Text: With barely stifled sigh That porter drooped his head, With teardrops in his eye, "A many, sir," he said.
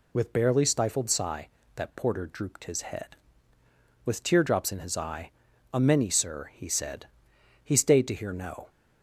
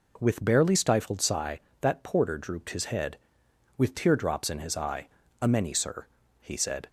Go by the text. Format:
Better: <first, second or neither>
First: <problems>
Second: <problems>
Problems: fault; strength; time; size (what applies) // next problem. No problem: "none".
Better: second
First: goes on to say "He stayed to hear no"; noticeable; from 7.6 s on; 1.0 s long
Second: none